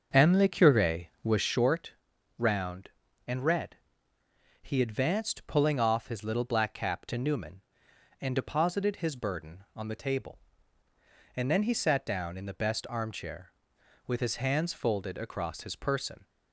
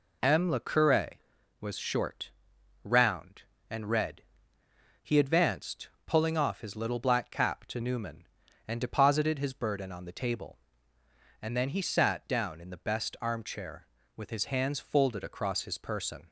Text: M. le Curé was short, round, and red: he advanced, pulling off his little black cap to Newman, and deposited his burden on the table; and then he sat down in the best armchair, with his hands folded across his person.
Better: second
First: starts louder than the rest; until 1.6 s; 6.5 dB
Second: none

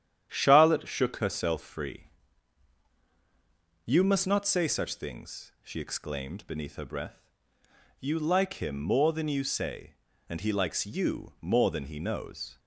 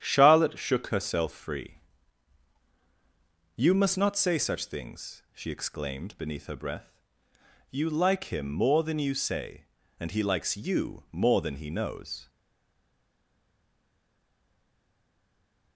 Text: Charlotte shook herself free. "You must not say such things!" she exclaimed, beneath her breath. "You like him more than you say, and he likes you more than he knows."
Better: first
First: starts louder than the rest; strong; until 1.3 s; 10 dB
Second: starts louder than the rest; strong; until 1.0 s; 10 dB // stays silent after the last word; strong; from 12.2 s on; 3.5 s long

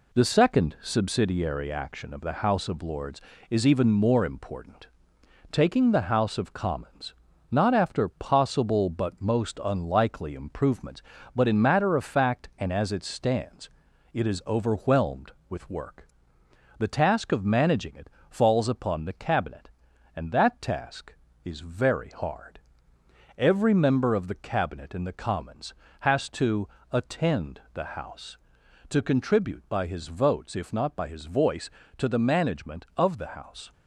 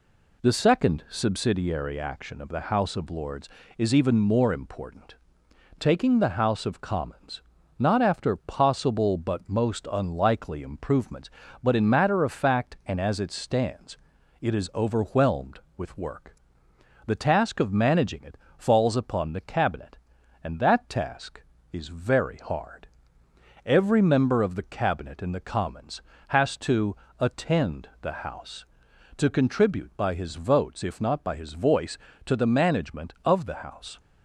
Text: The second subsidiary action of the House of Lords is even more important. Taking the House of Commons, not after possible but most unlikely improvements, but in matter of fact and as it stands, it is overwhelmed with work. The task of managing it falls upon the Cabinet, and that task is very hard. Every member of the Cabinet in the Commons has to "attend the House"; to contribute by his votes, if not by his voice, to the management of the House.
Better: second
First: gets quieter; noticeable; throughout; 4.5 dB // pauses between "it" and "falls"; slight; at 18.0 s; 0.20 s long // pauses between "to" and "attend"; slight; at 26.6 s; 0.24 s long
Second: pauses between "it" and "falls"; slight; at 18.3 s; 0.20 s long // pauses between "to" and "attend"; slight; at 26.9 s; 0.24 s long

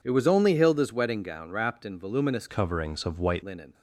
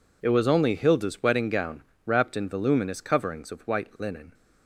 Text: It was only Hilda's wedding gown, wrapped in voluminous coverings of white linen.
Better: second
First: changes voice from "coverings" to "white"; from 2.4 to 3.4 s; 1.0 s long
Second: none

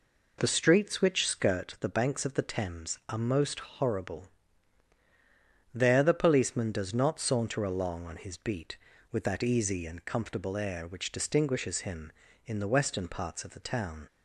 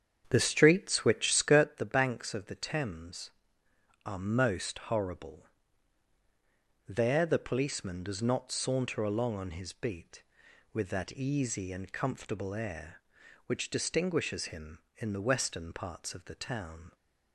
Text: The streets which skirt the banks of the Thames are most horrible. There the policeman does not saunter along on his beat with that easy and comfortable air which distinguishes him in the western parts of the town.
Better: first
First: none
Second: starts louder than the rest; strong; until 1.7 s; 8 dB

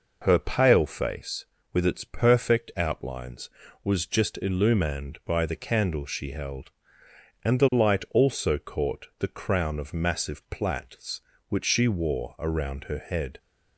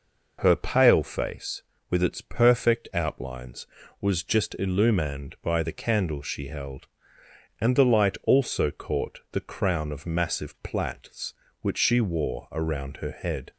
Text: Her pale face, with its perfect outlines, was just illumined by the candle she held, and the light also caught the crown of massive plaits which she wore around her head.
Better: neither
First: none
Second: none

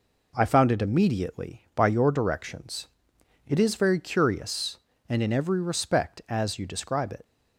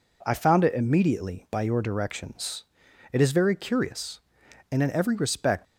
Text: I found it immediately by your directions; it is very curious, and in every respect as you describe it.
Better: first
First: none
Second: stops before "as you describe it"; at 5.6 s

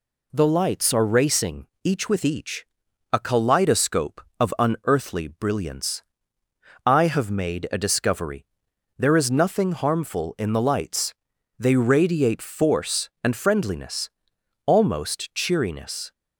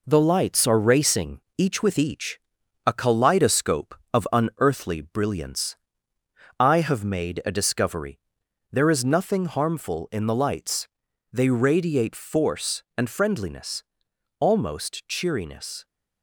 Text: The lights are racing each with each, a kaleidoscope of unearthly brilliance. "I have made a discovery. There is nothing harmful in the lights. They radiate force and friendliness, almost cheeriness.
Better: first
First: pauses between "racing" and "each"; slight; at 1.6 s; 0.16 s long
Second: gets quieter; noticeable; throughout; 4 dB // pauses between "racing" and "each"; slight; at 1.3 s; 0.16 s long

